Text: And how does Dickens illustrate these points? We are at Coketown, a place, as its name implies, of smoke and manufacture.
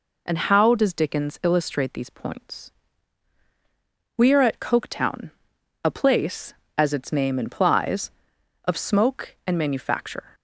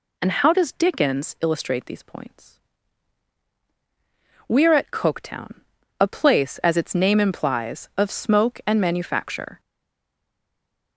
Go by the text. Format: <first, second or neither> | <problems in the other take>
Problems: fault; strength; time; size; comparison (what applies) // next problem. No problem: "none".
first | stays silent after the last word; noticeable; from 9.5 s on; 1.4 s long